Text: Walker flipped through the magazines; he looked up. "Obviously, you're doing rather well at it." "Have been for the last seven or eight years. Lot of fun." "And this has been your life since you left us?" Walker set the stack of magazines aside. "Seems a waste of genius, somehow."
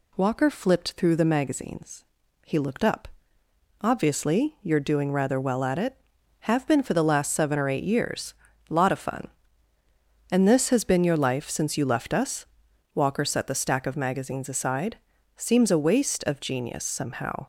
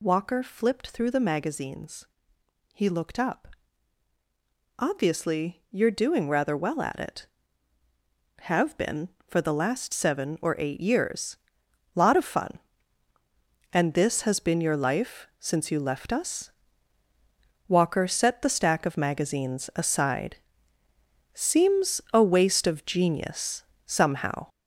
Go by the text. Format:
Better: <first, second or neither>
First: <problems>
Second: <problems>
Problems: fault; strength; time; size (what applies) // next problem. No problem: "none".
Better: first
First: none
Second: gets louder; strong; throughout; 7 dB